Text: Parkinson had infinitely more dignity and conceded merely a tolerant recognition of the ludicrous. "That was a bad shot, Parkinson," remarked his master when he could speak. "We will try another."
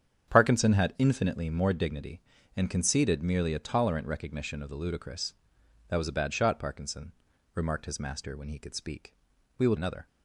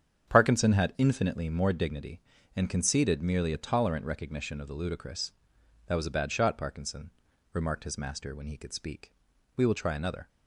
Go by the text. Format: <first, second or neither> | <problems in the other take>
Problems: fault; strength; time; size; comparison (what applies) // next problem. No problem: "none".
second | starts louder than the rest; strong; until 1.3 s; 8 dB; strong in the second // skips "try"; at 9.7 s